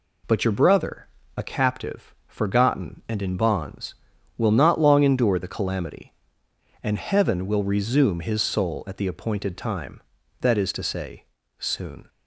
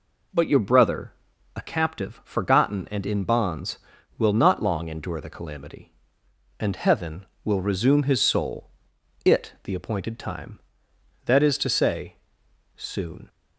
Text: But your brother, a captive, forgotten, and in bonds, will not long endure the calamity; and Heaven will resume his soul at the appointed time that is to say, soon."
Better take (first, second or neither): first